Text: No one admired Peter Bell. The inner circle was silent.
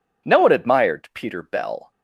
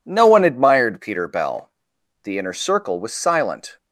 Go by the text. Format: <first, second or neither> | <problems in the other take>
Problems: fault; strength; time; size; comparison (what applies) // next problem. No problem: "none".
second | stops before "The inner circle was silent"; at 1.9 s